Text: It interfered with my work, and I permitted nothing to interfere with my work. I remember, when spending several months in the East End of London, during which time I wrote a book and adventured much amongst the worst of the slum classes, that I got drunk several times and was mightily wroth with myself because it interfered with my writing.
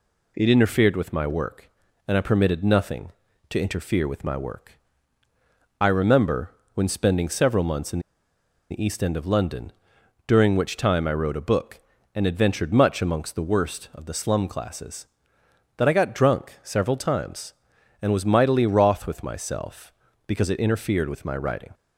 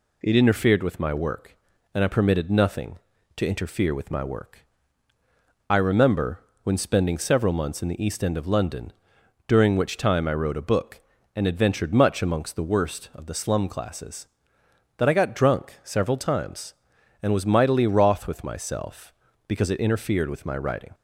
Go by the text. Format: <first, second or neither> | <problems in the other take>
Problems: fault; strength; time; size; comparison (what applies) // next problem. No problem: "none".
second | pauses between "in" and "the"; noticeable; at 7.9 s; 0.71 s long